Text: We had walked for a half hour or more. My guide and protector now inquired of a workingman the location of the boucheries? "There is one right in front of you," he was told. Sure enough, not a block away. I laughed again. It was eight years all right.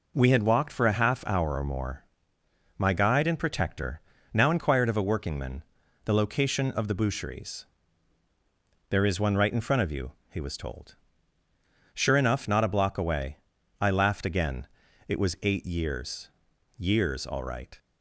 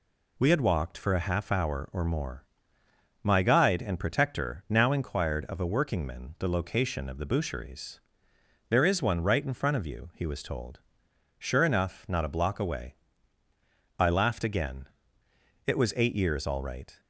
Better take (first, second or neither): second